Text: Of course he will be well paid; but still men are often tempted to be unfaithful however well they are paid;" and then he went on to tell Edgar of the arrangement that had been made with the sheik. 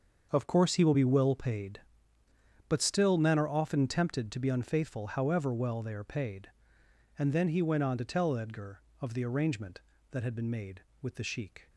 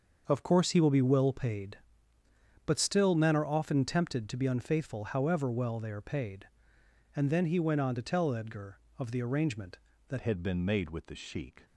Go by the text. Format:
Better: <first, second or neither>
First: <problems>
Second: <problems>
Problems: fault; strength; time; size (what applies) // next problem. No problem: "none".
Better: first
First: starts louder than the rest; until 1.3 s; 6.5 dB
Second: starts louder than the rest; until 1.2 s; 6.5 dB // changes voice at "had"; from 10.2 s on; 1.4 s long